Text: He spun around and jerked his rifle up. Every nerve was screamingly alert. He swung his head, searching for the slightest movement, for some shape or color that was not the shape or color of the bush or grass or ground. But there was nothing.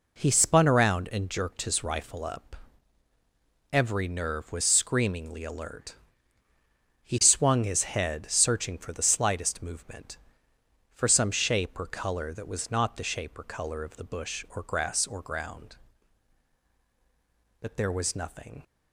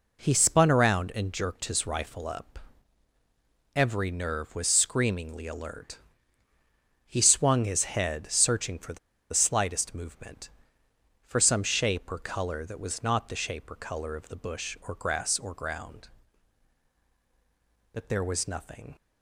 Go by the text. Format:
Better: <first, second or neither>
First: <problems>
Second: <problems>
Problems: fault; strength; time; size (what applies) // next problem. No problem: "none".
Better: first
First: none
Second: pauses between "the" and "slightest"; slight; at 8.9 s; 0.34 s long